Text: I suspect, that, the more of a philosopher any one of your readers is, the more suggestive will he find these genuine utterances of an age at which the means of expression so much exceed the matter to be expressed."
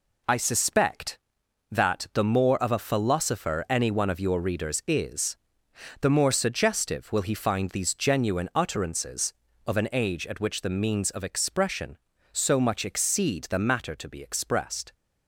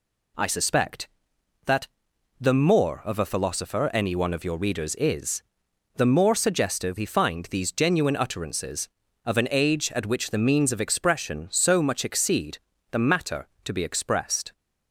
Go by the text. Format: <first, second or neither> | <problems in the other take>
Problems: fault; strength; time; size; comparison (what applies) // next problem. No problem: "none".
first | skips "will"; at 6.9 s // pauses between "exceed" and "the"; slight; at 12.5 s; 0.32 s long